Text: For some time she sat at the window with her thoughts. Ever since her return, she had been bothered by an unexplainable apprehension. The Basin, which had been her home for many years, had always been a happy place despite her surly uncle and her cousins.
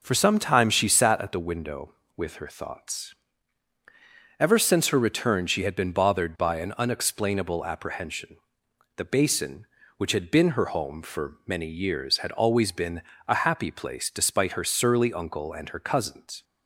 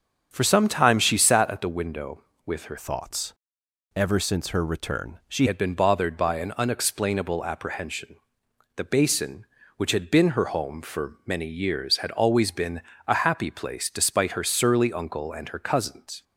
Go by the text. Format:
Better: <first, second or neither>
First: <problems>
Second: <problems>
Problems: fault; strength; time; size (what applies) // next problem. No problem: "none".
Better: first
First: pauses between "been" and "a"; slight; at 13.0 s; 0.26 s long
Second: starts louder than the rest; until 1.3 s; 6.5 dB // changes voice from "thoughts" to "she"; from 2.7 to 5.4 s; 2.7 s long // pauses between "been" and "a"; slight; at 12.8 s; 0.26 s long